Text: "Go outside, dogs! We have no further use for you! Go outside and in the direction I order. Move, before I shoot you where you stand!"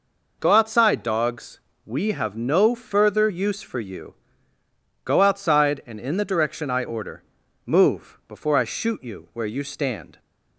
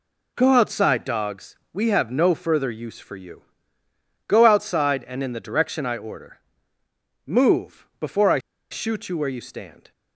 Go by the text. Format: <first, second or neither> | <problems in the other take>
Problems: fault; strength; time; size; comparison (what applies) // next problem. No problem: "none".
first | pauses between "I" and "shoot"; slight; at 8.3 s; 0.31 s long